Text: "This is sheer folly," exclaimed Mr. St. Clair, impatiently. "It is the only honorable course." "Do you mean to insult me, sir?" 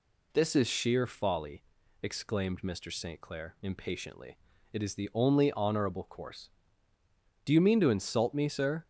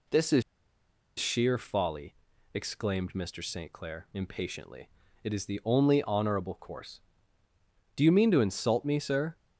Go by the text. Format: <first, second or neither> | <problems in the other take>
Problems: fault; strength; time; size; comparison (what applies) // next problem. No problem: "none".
first | pauses between "is" and "sheer"; noticeable; at 0.4 s; 0.77 s long